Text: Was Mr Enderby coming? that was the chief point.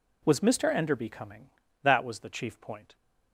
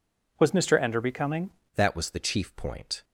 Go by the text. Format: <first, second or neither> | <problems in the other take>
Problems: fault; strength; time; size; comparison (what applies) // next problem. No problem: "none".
first | changes voice at "that"; from 1.7 s on; 1.3 s long